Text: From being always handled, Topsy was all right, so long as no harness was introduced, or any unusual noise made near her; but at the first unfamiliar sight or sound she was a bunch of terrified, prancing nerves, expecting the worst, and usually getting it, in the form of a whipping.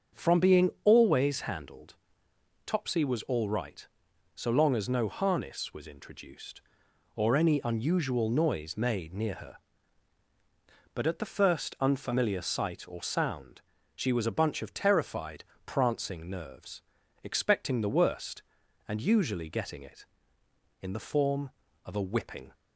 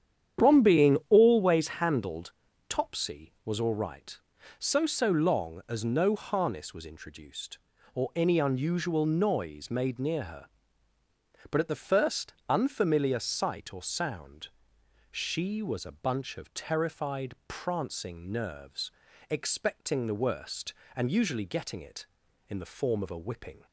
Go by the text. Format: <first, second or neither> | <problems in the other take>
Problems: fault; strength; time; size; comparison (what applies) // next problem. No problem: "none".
first | starts louder than the rest; strong; until 1.5 s; 9.5 dB; also in the first // says "so" twice; at 4.8 s // pauses between "first" and "unfamiliar"; slight; at 12.3 s; 0.16 s long // pauses between "sound" and "she"; noticeable; at 14.4 s; 0.64 s long; slight in the first